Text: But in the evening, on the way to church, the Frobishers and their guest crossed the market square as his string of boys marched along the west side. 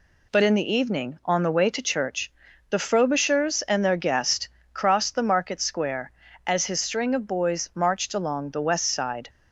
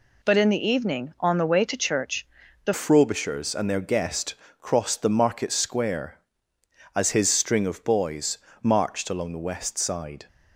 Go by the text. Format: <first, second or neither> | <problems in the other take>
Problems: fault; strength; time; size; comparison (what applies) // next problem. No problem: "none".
first | changes voice at "Frobishers"; from 2.7 s on; 7.5 s long // pauses between "guest" and "crossed"; slight; at 4.3 s; 0.24 s long; slight in the first // pauses between "boys" and "marched"; slight; at 8.3 s; 0.24 s long